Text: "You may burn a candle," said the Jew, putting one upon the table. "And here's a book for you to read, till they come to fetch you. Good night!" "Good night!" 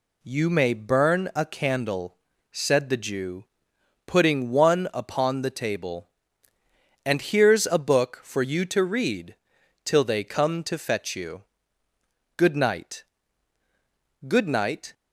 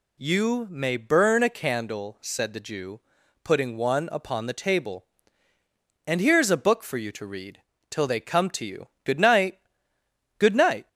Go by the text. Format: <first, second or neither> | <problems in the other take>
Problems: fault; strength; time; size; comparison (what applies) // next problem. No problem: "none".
first | skips "fetch"; at 8.6 s